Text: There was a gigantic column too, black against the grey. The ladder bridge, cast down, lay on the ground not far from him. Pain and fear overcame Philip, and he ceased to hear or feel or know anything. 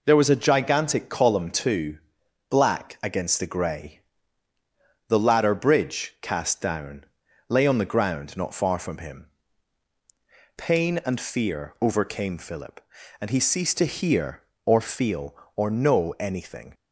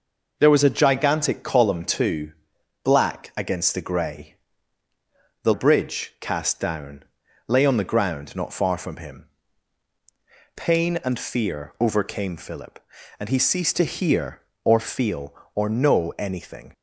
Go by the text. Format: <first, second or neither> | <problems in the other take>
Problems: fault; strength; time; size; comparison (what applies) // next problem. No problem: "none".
first | skips "ladder"; at 5.5 s